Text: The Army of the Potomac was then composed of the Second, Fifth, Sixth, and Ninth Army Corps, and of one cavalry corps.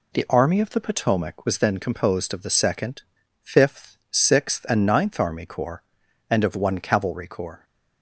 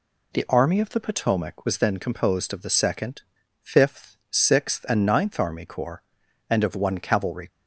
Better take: first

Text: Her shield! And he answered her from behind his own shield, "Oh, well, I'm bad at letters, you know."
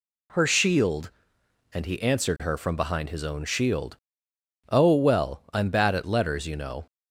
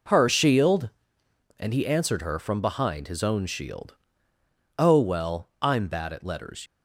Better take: first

